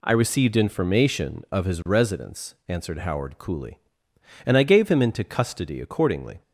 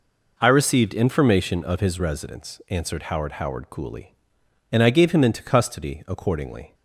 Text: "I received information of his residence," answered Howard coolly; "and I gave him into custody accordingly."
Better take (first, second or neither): first